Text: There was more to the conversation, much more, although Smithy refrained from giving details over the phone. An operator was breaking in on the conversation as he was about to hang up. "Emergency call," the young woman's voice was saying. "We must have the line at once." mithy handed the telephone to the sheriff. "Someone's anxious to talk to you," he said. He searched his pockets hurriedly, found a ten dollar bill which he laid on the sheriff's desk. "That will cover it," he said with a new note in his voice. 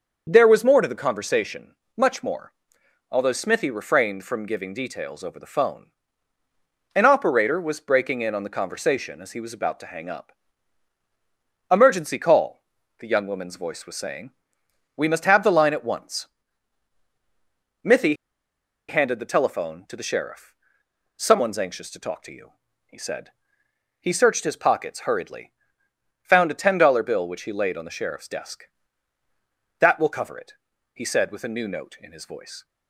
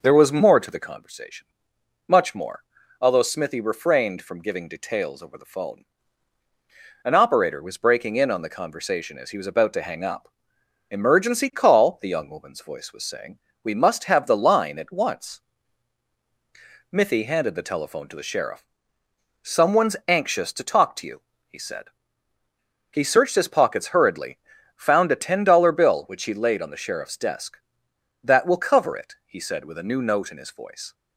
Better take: second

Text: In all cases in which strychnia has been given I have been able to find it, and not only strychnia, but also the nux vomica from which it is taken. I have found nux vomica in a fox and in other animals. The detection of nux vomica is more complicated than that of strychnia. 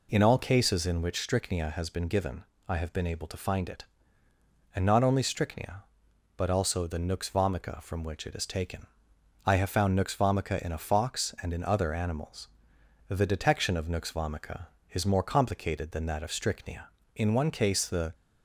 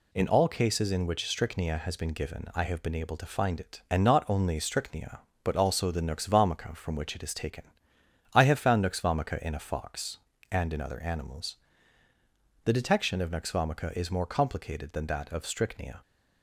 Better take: second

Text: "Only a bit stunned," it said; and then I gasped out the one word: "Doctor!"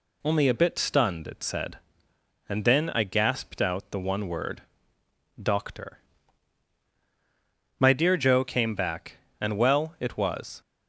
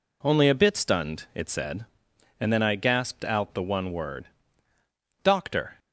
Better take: second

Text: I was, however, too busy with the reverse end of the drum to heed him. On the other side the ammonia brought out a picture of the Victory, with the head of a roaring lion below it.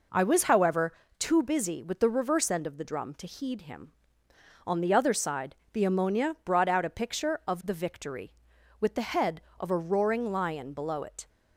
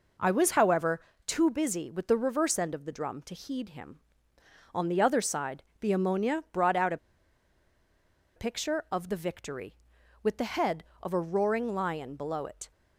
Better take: first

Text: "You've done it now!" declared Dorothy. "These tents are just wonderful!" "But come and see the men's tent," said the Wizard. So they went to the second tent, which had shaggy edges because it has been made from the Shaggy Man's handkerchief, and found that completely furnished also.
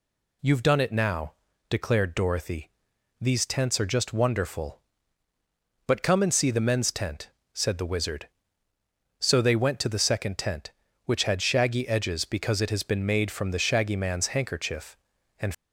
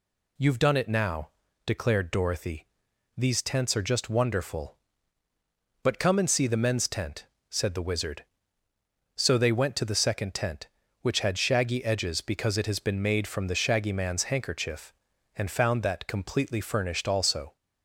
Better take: second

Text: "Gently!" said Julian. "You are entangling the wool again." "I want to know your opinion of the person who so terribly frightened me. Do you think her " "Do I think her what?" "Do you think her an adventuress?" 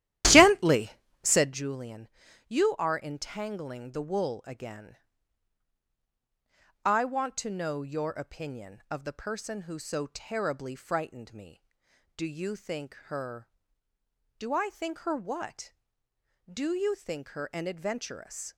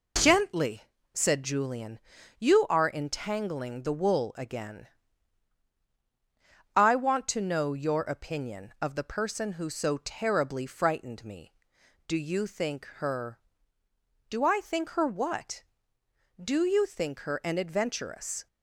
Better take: second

